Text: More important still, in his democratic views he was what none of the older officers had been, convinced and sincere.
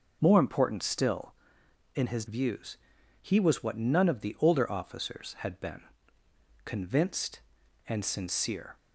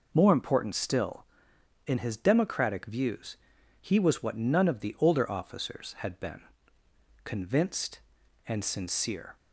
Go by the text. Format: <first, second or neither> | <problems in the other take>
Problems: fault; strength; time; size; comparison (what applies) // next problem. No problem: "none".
second | skips "democratic"; at 2.2 s // pauses between "views" and "he"; at 2.7 s; 0.44 s long; also in the second